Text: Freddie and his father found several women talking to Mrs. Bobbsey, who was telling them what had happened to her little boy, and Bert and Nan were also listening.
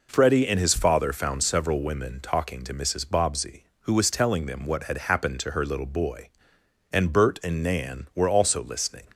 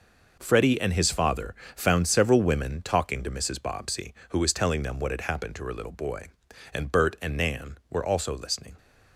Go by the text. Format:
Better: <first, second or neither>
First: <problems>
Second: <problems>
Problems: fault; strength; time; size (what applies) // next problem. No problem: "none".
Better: first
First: none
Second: gets quieter; strong; throughout; 9.5 dB // pauses between "father" and "found"; slight; at 1.5 s; 0.22 s long